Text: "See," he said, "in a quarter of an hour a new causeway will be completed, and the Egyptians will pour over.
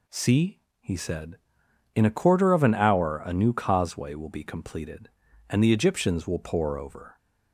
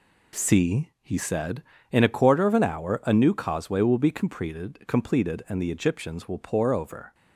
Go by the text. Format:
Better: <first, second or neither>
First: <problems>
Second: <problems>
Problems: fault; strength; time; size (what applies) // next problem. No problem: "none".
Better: first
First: none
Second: says "completed" twice; at 4.8 s